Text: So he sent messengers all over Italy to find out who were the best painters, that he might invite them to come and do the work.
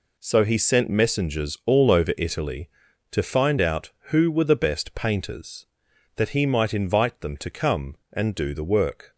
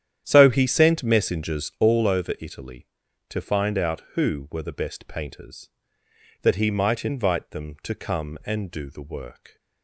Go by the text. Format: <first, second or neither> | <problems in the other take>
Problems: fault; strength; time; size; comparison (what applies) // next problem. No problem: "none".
first | starts louder than the rest; strong; until 1.9 s; 10 dB